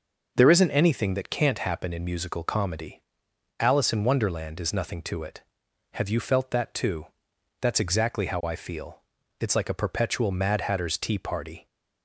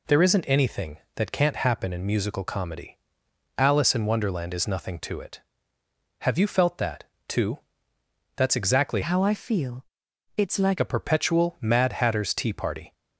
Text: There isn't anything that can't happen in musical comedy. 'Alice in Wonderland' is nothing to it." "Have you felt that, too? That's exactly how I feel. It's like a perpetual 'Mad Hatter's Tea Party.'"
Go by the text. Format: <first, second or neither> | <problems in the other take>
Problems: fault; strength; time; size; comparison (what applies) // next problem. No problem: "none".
first | changes voice from "how" to "like"; from 9.0 to 10.7 s; 1.7 s long